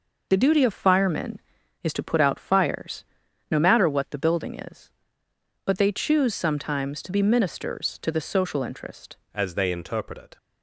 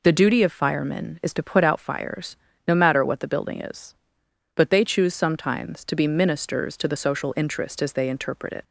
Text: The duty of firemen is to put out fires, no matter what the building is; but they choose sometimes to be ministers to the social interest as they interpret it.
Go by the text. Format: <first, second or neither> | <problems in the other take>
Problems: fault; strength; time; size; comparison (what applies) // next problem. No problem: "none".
second | changes voice at "as"; from 9.3 s on; 1.0 s long